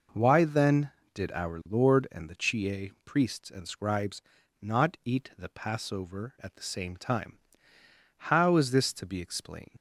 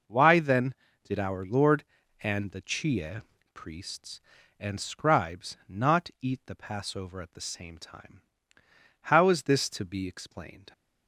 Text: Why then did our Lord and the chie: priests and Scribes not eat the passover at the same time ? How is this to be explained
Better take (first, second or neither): second